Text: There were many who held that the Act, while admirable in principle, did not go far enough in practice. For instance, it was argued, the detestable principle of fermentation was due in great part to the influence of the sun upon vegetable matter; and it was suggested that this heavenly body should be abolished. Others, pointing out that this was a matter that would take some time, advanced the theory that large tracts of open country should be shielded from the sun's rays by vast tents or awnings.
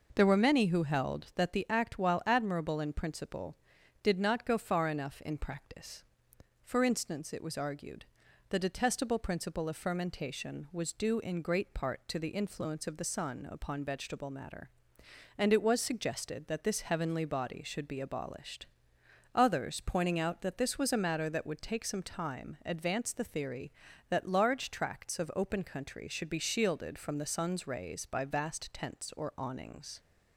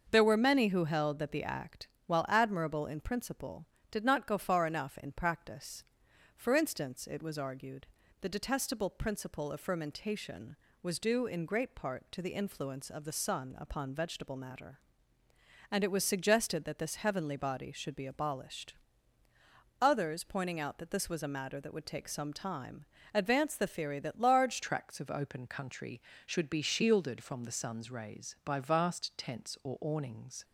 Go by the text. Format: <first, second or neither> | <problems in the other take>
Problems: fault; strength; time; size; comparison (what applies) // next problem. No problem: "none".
first | starts louder than the rest; until 1.1 s; 6.5 dB // changes voice at "tracts"; from 24.6 s on; 5.8 s long